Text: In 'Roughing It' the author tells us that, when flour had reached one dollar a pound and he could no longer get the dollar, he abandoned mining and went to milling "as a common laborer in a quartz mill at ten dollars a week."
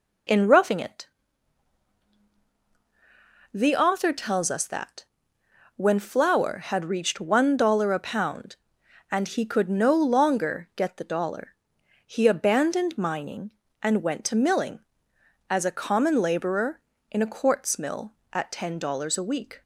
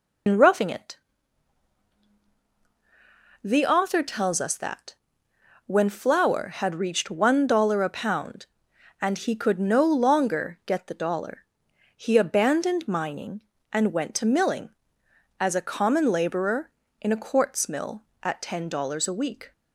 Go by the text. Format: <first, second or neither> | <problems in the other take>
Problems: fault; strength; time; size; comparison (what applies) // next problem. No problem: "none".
first | loses the start of "In"; at 0.2 s; 90 ms // pauses between "It" and "the"; strong; at 0.9 s; 2.4 s long; strong in the first